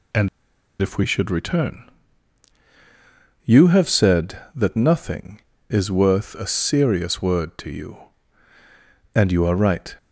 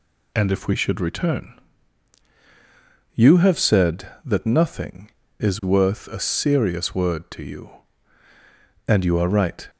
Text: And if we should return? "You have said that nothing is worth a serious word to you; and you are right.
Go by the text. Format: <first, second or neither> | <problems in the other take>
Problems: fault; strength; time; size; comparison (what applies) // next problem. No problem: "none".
second | pauses between "And" and "if"; noticeable; at 0.2 s; 0.52 s long